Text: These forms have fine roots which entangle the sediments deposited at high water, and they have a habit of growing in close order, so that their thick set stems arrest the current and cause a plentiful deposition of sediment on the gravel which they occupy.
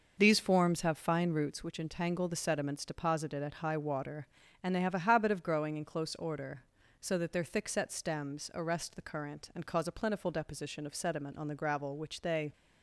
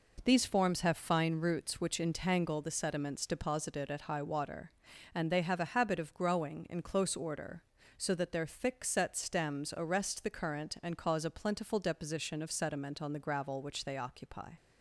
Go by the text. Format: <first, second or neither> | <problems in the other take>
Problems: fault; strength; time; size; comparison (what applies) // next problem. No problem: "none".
second | stops before "occupy"; at 12.5 s